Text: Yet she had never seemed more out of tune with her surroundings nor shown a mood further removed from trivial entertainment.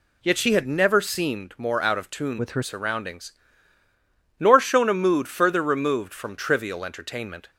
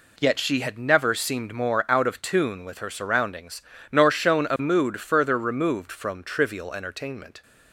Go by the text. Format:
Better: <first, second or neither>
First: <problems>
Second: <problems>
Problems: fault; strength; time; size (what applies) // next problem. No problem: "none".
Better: second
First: changes voice from "with" to "her"; from 2.3 to 2.6 s; 0.3 s long // pauses between "surroundings" and "nor"; at 3.3 s; 1.1 s long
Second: pauses between "surroundings" and "nor"; slight; at 3.6 s; 0.28 s long